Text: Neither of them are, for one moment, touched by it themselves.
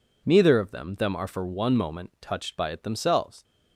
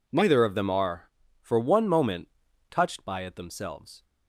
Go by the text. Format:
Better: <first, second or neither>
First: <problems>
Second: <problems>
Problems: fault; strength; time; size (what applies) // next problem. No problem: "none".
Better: second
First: says "them" twice; at 0.9 s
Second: none